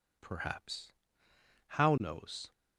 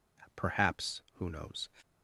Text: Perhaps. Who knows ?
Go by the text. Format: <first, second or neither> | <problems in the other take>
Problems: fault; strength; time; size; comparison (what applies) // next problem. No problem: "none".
second | says "How" for "Who"; at 1.6 s